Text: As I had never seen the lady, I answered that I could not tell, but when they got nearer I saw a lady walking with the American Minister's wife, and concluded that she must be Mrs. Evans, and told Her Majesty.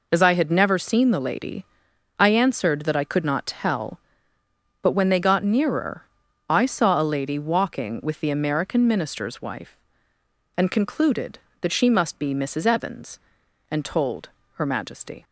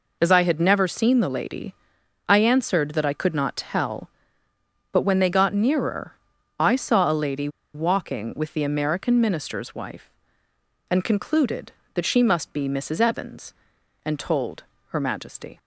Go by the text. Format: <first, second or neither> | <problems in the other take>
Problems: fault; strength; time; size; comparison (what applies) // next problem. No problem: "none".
first | pauses between "nearer" and "I"; at 6.1 s; 0.44 s long; also in the first // pauses between "lady" and "walking"; slight; at 7.4 s; 0.25 s long // pauses between "told" and "Her"; slight; at 14.6 s; 0.28 s long; slight in the first